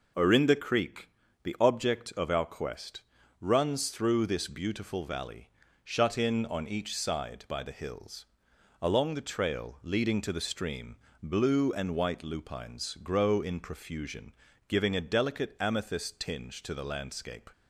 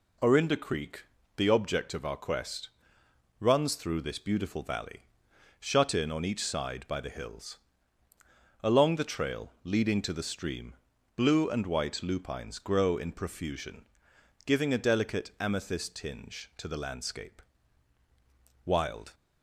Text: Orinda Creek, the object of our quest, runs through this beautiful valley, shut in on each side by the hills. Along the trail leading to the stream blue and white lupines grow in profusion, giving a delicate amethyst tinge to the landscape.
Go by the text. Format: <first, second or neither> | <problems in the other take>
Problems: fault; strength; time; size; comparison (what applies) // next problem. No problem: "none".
first | pauses between "stream" and "blue"; at 10.7 s; 0.40 s long; slight in the first // goes on to say "Wild"; slight; from 18.6 s on; 0.48 s long